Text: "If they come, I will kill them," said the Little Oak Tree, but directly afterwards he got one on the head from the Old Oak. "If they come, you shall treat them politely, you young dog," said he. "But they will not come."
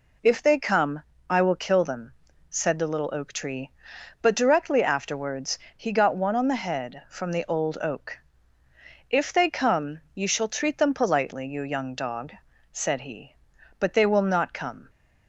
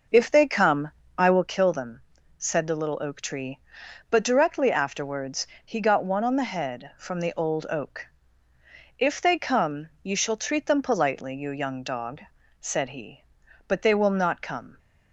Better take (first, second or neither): first